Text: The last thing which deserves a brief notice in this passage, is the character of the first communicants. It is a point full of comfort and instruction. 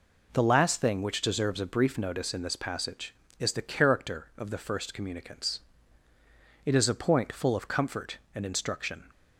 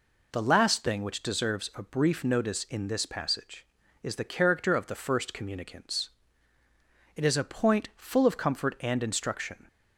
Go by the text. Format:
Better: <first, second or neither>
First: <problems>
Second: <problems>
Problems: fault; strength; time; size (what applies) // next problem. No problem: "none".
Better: neither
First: none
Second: none